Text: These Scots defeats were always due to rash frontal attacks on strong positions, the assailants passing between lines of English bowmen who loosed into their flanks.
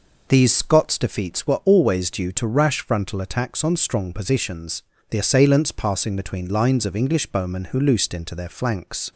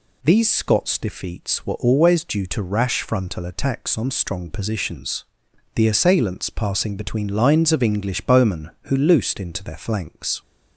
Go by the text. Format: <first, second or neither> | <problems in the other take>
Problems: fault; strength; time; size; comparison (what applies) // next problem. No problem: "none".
neither | none